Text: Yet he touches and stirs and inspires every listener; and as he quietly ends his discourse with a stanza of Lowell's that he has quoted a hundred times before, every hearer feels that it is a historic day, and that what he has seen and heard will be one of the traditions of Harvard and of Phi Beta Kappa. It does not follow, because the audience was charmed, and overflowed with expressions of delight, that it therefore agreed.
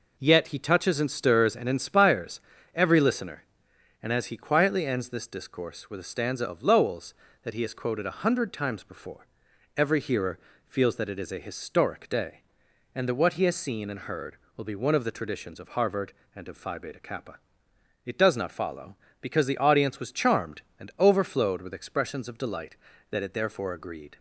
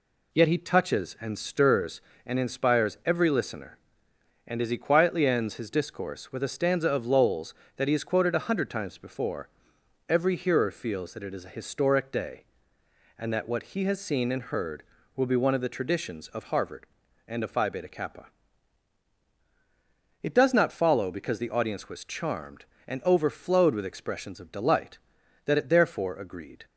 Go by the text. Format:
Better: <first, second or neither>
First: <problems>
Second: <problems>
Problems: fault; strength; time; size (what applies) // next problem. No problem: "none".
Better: second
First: pauses between "inspires" and "every"; slight; at 2.4 s; 0.34 s long // says "this" for "his"; at 5.1 s // pauses between "hearer" and "feels"; slight; at 10.3 s; 0.28 s long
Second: none